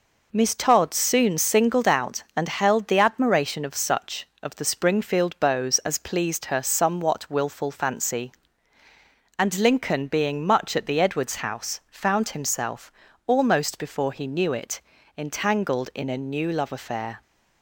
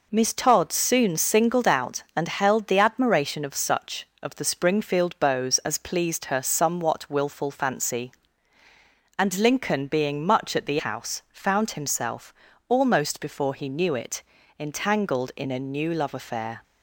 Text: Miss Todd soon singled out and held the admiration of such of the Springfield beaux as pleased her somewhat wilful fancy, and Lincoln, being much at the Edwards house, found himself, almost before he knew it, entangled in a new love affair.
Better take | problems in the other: first | skips "Edwards"; at 10.7 s

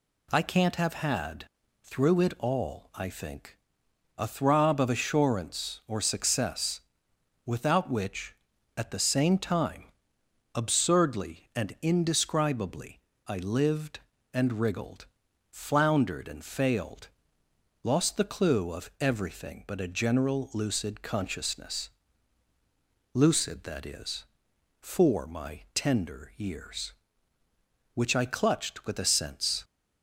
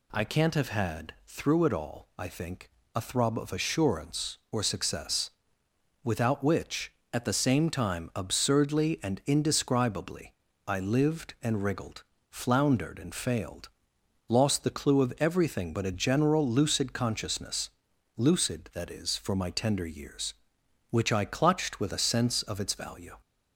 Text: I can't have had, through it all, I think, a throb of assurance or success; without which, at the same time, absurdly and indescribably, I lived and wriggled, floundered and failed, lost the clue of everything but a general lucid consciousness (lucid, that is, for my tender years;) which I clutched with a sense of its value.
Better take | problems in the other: second | stops before "of its value"; at 29.6 s

